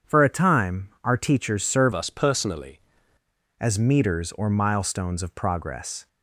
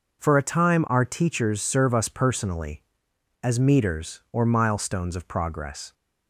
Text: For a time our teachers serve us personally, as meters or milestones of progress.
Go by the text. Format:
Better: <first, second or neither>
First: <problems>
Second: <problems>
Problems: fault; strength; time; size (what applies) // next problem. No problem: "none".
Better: second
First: starts louder than the rest; strong; until 1.2 s; 7.5 dB // changes voice from "us" to "personally"; from 1.9 to 2.7 s; 0.8 s long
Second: none